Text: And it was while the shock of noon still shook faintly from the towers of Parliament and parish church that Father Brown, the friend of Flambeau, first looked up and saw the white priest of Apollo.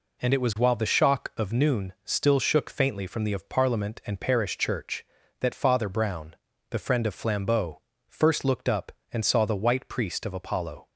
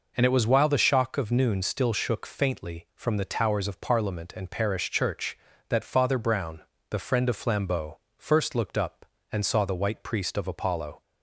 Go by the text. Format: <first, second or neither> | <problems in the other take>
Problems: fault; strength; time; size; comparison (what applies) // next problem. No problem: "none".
second | skips "towers"; at 3.3 s